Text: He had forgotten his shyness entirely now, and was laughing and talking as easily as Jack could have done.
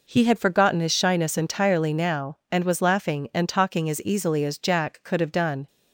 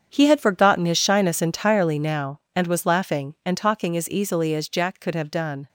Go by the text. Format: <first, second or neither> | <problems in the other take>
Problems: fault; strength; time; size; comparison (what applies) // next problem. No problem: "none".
first | gets quieter; strong; throughout; 12.5 dB